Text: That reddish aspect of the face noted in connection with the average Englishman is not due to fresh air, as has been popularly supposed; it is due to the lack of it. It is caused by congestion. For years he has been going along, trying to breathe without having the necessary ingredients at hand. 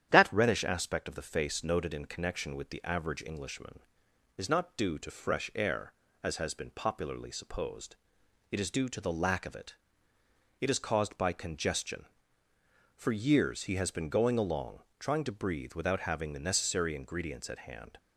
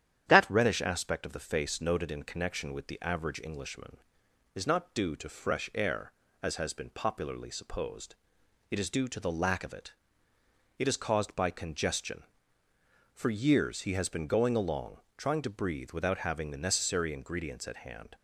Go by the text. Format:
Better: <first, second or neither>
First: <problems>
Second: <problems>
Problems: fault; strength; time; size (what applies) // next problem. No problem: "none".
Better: neither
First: starts louder than the rest; strong; until 1.1 s; 10 dB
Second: starts louder than the rest; strong; until 1.3 s; 10 dB